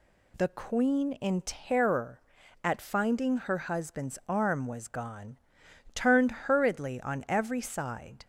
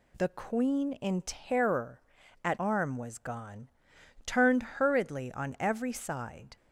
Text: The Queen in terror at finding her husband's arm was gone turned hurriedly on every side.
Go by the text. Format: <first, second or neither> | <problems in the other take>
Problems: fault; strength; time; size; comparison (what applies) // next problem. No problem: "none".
first | skips "finding her husband's"; at 2.5 s // pauses between "gone" and "turned"; noticeable; at 3.6 s; 0.58 s long; noticeable in the first